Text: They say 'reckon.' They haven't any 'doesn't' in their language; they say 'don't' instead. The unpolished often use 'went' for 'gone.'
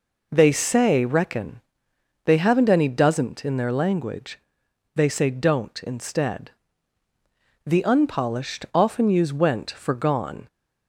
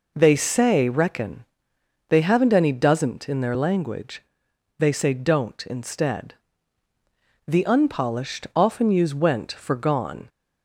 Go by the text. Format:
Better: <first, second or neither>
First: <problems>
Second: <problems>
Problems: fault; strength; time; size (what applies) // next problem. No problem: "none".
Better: neither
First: none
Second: none